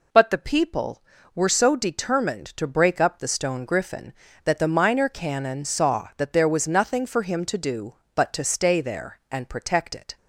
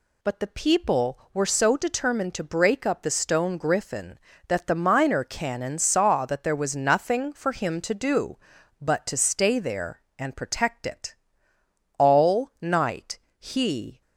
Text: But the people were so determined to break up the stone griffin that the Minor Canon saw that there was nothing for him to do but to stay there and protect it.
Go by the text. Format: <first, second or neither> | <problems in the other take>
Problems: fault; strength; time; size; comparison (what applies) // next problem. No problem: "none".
first | goes on to say "All night he"; strong; from 11.9 s on; 2.0 s long